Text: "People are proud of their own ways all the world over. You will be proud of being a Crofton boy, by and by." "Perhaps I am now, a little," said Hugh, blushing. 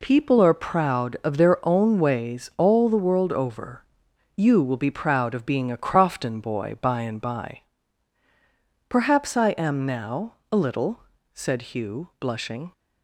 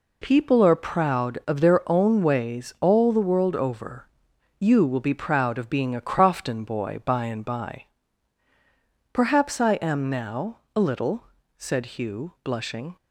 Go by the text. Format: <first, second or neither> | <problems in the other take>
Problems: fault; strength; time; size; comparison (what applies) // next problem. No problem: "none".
neither | none